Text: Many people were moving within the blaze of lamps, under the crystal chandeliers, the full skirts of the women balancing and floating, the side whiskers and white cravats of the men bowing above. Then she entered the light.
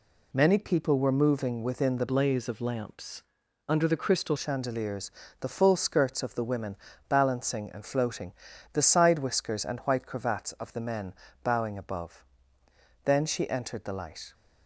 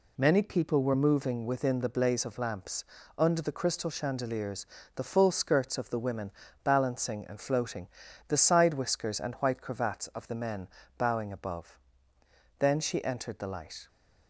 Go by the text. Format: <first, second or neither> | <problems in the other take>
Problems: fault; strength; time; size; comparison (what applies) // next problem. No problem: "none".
second | changes voice from "blaze" to "crystal"; from 2.0 to 4.3 s; 2.3 s long // pauses between "women" and "balancing"; slight; at 6.7 s; 0.32 s long; slight in the second // pauses between "men" and "bowing"; slight; at 11.1 s; 0.30 s long; slight in the second